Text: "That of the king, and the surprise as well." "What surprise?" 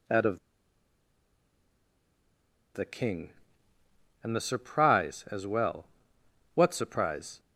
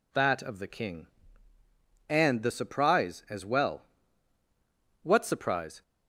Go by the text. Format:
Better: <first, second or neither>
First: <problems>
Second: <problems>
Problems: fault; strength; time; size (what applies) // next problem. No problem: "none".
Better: second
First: pauses between "of" and "the"; strong; at 0.3 s; 2.3 s long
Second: none